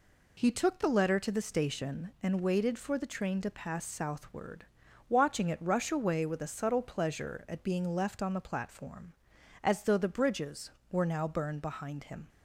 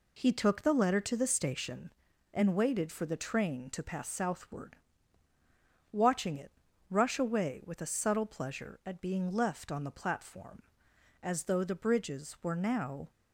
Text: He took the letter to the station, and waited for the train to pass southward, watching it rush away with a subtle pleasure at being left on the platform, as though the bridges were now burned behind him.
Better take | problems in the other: first | pauses between "it" and "rush"; at 6.4 s; 0.40 s long // stops before "burned behind him"; at 13.0 s

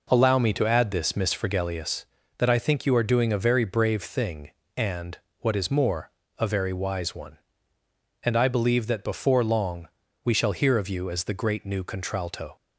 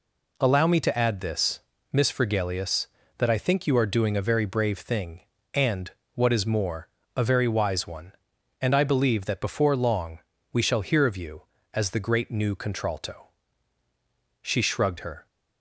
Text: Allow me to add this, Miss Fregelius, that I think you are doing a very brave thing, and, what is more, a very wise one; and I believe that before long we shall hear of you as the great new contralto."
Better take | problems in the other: first | pauses between "long" and "we"; slight; at 10.1 s; 0.32 s long; slight in the first // goes on to say "She shrugged her"; noticeable; from 14.4 s on; 0.84 s long

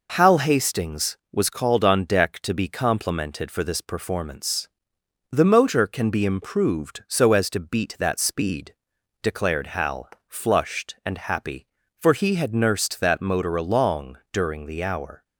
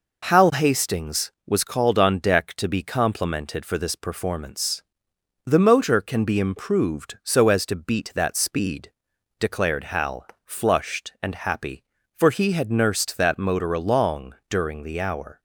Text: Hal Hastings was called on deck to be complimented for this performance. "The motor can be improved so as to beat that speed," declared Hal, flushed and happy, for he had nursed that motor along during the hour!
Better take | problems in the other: neither | pauses between "along" and "during"; slight; the same in both

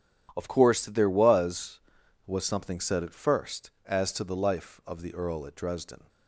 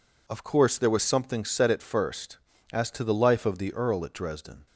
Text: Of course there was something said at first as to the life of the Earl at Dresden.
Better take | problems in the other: second | starts louder than the rest; strong; until 1.3 s; 10.5 dB // says "was" twice; at 2.2 s

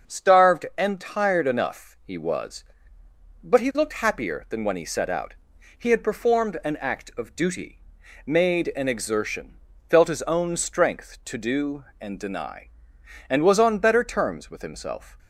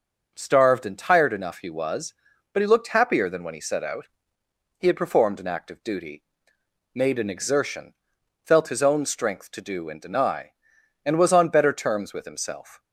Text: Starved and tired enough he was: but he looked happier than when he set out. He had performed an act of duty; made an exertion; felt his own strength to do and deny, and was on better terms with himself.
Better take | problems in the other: neither | starts louder than the rest; the same in both

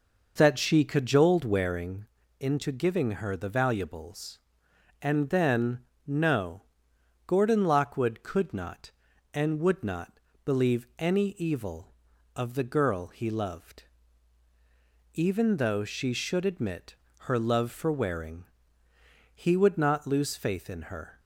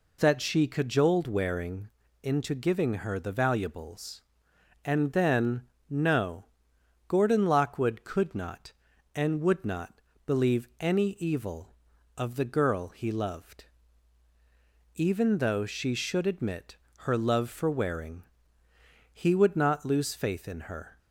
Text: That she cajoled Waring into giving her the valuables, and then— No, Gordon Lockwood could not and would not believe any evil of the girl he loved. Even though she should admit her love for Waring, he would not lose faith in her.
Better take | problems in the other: second | starts louder than the rest; noticeable; until 1.7 s; 5.5 dB // pauses between "Waring" and "into"; slight; at 2.0 s; 0.34 s long; slight in the second // pauses between "not" and "believe"; slight; at 10.2 s; 0.24 s long; slight in the second // pauses between "admit" and "her"; slight; at 16.9 s; 0.22 s long; slight in the second

